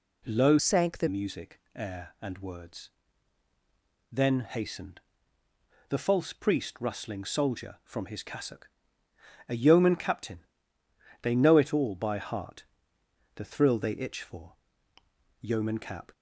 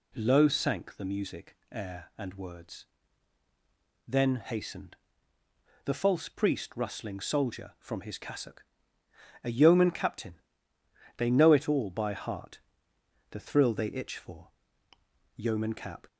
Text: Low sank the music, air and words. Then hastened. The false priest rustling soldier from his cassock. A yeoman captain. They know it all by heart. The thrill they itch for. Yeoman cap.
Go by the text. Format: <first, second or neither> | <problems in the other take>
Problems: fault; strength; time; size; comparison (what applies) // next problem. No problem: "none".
second | changes voice from "sank" to "the"; from 0.5 to 1.0 s; 0.5 s long